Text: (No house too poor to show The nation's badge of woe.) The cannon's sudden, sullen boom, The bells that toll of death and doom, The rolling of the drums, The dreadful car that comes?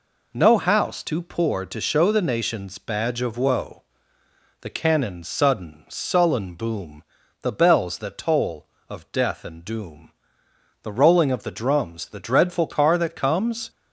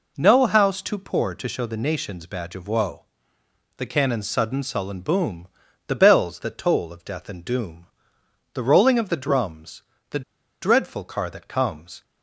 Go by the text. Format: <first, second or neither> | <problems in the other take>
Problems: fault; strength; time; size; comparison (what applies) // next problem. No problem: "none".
first | pauses between "The" and "dreadful"; at 10.2 s; 0.40 s long